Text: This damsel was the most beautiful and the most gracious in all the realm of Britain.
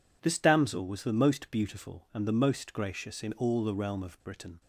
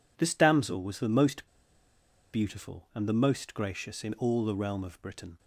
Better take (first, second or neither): first